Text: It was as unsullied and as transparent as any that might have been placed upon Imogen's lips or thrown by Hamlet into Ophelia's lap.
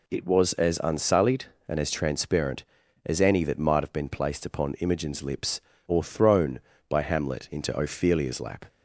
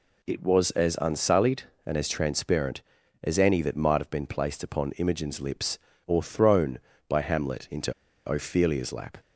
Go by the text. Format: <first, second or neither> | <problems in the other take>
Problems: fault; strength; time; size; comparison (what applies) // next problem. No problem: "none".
first | pauses between "into" and "Ophelia's"; at 7.9 s; 0.37 s long